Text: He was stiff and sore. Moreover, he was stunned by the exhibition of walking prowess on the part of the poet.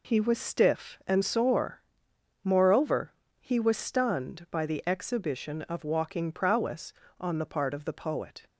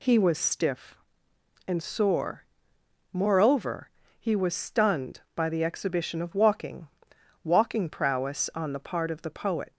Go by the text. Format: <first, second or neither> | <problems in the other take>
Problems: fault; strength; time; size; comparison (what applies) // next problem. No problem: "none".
first | says "walking" twice; at 7.4 s